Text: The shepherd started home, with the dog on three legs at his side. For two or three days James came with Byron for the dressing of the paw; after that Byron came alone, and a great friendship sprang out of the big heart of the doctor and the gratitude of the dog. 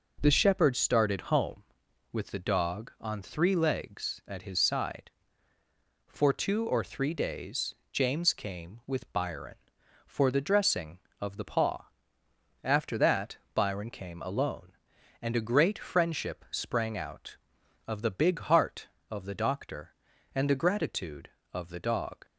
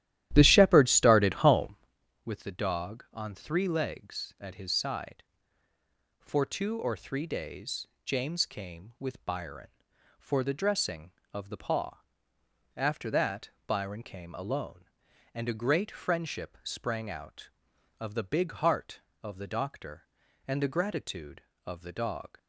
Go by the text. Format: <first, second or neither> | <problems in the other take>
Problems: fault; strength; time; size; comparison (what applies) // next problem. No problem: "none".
first | starts louder than the rest; strong; until 2.0 s; 13 dB // pauses between "days" and "James"; slight; at 7.8 s; 0.20 s long; slight in the first // pauses between "that" and "Byron"; slight; at 13.4 s; 0.16 s long; slight in the first